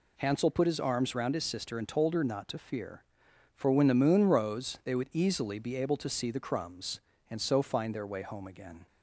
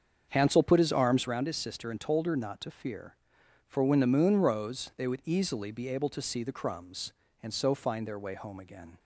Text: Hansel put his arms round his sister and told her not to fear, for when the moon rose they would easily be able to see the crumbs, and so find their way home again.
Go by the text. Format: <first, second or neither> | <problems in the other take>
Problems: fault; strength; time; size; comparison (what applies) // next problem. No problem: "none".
first | starts louder than the rest; until 1.3 s; 7 dB